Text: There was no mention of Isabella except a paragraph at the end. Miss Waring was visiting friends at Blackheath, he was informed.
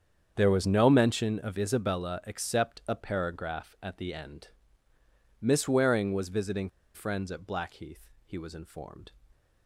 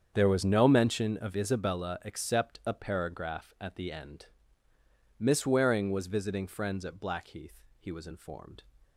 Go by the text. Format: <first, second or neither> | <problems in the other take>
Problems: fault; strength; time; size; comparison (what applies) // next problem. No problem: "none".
second | starts louder than the rest; strong; until 1.3 s; 7.5 dB; strong in the second // pauses between "visiting" and "friends"; slight; at 6.6 s; 0.26 s long